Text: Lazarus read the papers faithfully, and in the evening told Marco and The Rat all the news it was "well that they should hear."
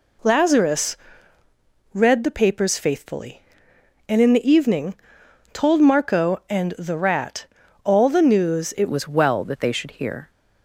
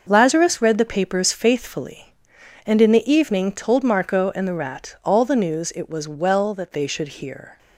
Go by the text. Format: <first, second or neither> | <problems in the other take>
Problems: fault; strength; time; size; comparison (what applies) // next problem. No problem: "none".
second | pauses between "Lazarus" and "read"; noticeable; at 0.9 s; 0.96 s long // pauses between "evening" and "told"; noticeable; at 4.9 s; 0.60 s long // pauses between "Rat" and "all"; at 7.4 s; 0.38 s long // changes voice at "was"; from 8.9 s on; 1.4 s long